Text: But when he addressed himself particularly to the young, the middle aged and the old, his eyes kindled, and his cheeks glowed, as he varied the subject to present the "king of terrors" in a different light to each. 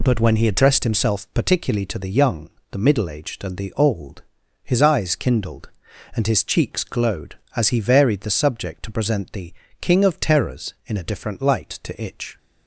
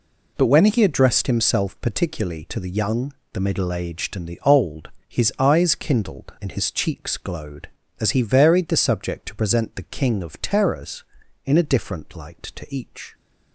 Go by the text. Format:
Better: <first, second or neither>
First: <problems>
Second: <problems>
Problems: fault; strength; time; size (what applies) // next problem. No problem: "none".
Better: second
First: pauses between "the" and "king"; slight; at 9.5 s; 0.26 s long // says "itch" for "each"; at 12.0 s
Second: none